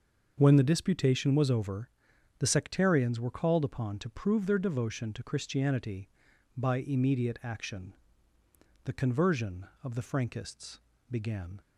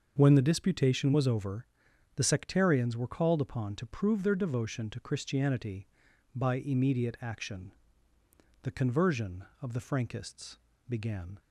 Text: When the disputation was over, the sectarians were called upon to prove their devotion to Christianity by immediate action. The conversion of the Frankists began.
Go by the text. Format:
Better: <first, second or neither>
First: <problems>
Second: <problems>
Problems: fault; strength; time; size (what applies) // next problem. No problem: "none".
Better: neither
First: starts louder than the rest; until 1.3 s; 6 dB // pauses between "Frankists" and "began"; slight; at 10.7 s; 0.32 s long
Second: starts louder than the rest; until 1.1 s; 6 dB // pauses between "Frankists" and "began"; slight; at 10.5 s; 0.32 s long